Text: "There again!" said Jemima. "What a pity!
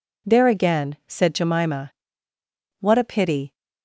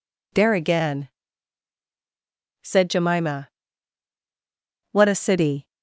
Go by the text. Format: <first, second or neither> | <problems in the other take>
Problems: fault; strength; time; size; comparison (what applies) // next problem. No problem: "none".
first | says "city" for "pity"; at 5.1 s